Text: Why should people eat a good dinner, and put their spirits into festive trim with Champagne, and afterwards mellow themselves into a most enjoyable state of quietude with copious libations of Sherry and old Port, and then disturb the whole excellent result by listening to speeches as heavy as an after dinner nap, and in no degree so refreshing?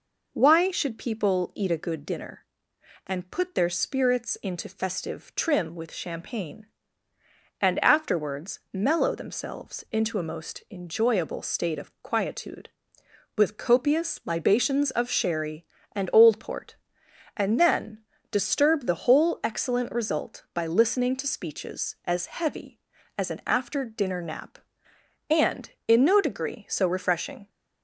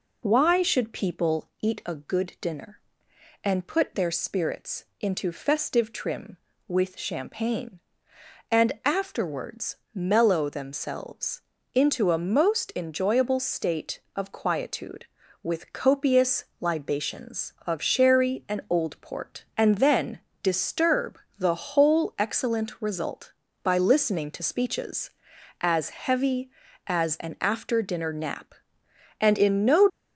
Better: first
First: pauses between "then" and "disturb"; slight; at 17.9 s; 0.32 s long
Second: pauses between "afterwards" and "mellow"; slight; at 9.7 s; 0.18 s long // pauses between "themselves" and "into"; slight; at 11.4 s; 0.32 s long // pauses between "copious" and "libations"; slight; at 16.4 s; 0.16 s long // pauses between "then" and "disturb"; slight; at 20.1 s; 0.22 s long // pauses between "disturb" and "the"; slight; at 21.1 s; 0.20 s long // stops before "degree so refreshing"; at 29.8 s

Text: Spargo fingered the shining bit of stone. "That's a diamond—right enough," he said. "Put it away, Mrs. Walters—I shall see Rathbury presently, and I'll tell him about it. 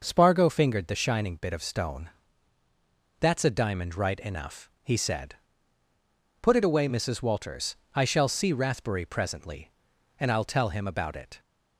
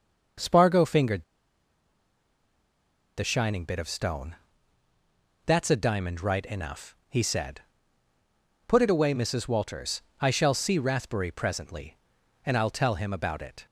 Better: first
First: none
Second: pauses between "fingered" and "the"; strong; at 1.2 s; 1.9 s long

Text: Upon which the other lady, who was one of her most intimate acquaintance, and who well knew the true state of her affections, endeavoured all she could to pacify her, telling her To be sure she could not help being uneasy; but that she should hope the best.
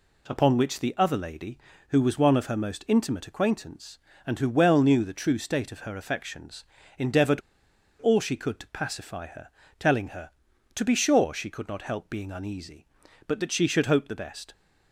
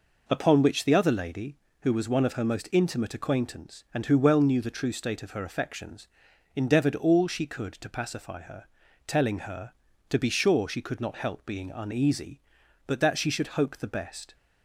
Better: second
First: pauses between "endeavoured" and "all"; noticeable; at 7.4 s; 0.59 s long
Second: none

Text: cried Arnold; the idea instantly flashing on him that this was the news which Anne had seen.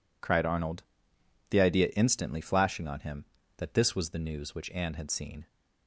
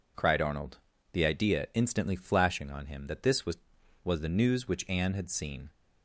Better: first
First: none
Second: says "was" twice; at 4.0 s

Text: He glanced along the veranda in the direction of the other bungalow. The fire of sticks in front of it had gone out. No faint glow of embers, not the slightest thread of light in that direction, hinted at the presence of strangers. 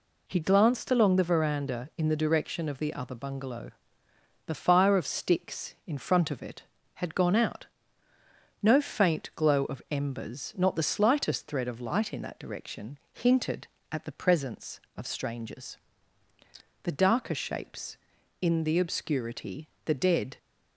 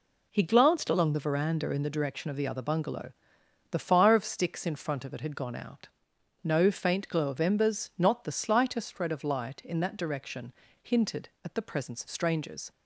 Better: second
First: goes on to say "The darker shapes in the obscurity the dead"; strong; from 16.8 s on; 3.5 s long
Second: none

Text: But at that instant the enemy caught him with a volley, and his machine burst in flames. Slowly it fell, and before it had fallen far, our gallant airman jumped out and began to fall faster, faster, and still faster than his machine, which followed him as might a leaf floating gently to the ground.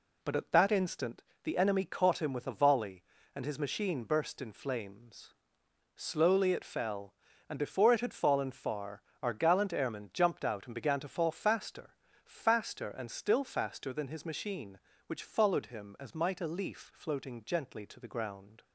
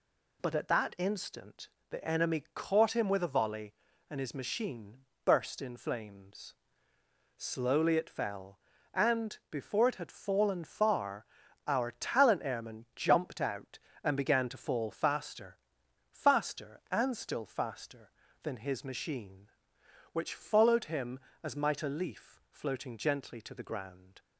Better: first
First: pauses between "instant" and "the"; slight; at 1.2 s; 0.22 s long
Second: pauses between "instant" and "the"; slight; at 1.6 s; 0.22 s long // pauses between "machine" and "burst"; slight; at 4.9 s; 0.26 s long // says "talent" for "gallant"; at 11.9 s

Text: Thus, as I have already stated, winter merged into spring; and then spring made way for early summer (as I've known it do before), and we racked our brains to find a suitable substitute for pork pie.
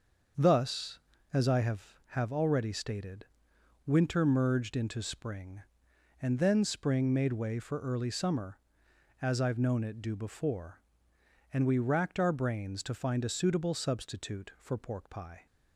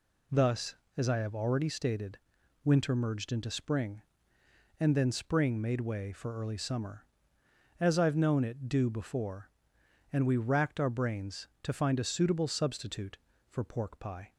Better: second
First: starts louder than the rest; until 1.7 s; 6.5 dB // says "have" twice; at 2.0 s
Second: none

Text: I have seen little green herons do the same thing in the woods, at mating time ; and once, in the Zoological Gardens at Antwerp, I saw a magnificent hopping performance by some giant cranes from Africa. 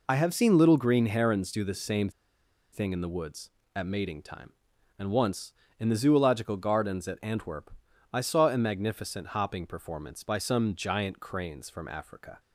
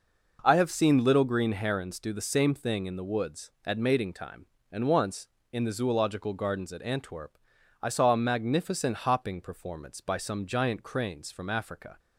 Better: second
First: pauses between "same" and "thing"; noticeable; at 2.0 s; 0.62 s long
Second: none

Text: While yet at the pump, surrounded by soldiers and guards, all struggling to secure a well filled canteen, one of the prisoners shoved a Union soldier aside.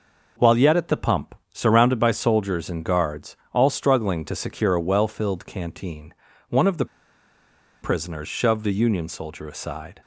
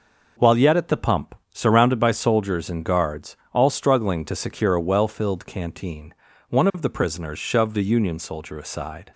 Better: second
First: pauses between "the" and "prisoners"; noticeable; at 6.8 s; 0.96 s long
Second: none

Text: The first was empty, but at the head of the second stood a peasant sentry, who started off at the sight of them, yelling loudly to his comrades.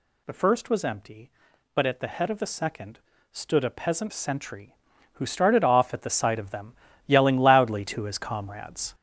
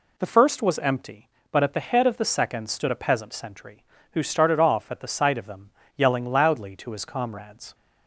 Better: second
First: gets louder; throughout; 7 dB // pauses between "second" and "stood"; slight; at 2.9 s; 0.32 s long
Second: none

